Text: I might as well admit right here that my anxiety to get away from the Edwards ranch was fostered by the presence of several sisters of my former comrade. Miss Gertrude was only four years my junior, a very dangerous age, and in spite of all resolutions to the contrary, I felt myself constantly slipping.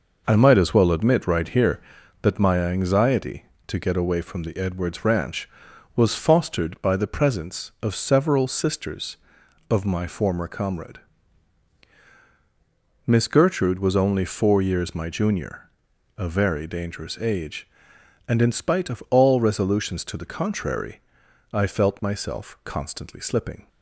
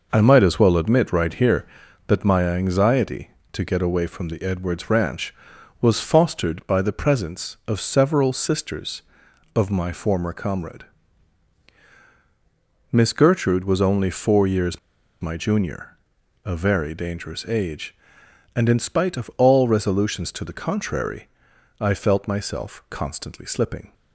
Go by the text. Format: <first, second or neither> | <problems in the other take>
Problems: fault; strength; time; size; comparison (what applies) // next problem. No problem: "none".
first | pauses between "years" and "my"; at 14.7 s; 0.42 s long